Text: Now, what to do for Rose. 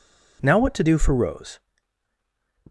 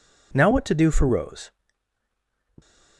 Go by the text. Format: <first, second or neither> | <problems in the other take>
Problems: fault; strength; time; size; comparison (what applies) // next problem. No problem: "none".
neither | none